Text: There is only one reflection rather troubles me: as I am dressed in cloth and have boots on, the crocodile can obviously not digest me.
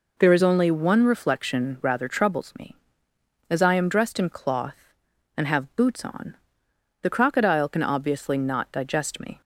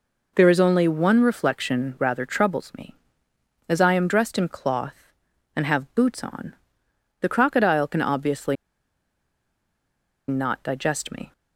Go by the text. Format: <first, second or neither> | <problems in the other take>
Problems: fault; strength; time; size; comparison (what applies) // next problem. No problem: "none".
first | pauses between "obviously" and "not"; strong; at 8.5 s; 1.7 s long